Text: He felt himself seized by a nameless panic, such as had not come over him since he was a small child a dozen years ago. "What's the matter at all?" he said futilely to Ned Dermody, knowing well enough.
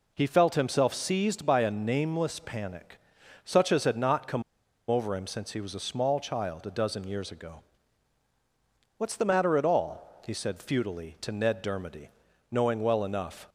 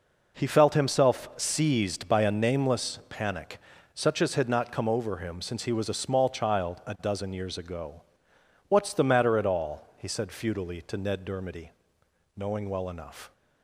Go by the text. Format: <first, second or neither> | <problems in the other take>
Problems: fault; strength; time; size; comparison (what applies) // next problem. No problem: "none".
second | pauses between "come" and "over"; noticeable; at 4.4 s; 0.48 s long